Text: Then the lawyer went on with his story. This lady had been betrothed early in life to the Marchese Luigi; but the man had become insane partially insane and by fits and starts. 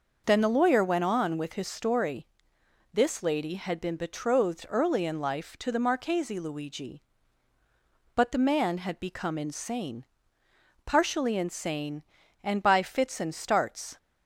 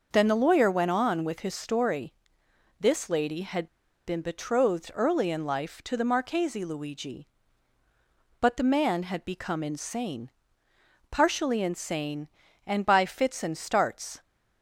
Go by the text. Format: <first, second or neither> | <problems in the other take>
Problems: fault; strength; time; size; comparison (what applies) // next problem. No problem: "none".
first | starts louder than the rest; noticeable; until 1.1 s; 6 dB; noticeable in the first // pauses between "had" and "been"; at 3.6 s; 0.39 s long // pauses between "insane" and "partially"; noticeable; at 10.3 s; 0.80 s long; noticeable in the first